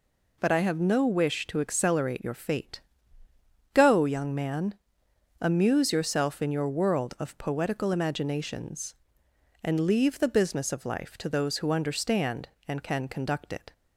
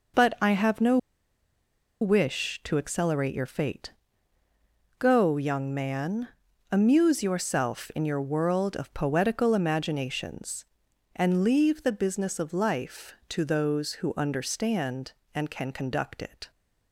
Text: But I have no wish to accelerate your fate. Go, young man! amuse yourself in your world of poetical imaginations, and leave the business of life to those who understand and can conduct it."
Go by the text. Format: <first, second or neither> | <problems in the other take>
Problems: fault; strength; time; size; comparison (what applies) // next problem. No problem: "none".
first | pauses between "no" and "wish"; at 0.9 s; 1.0 s long